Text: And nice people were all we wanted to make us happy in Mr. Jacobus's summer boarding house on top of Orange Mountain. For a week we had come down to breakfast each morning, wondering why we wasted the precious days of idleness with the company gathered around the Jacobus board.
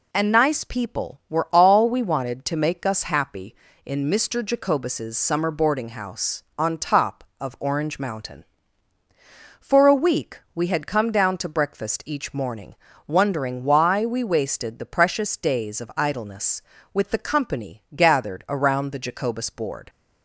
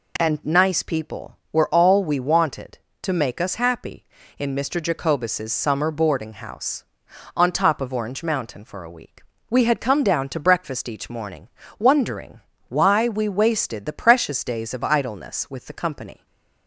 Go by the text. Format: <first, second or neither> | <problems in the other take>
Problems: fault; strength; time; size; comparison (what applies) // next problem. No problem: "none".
first | pauses between "week" and "we"; slight; at 9.2 s; 0.28 s long; slight in the first // pauses between "wondering" and "why"; slight; at 12.4 s; 0.28 s long // stays silent after the last word; slight; from 16.1 s on; 0.5 s long // stops before "gathered around the Jacobus board"; at 16.2 s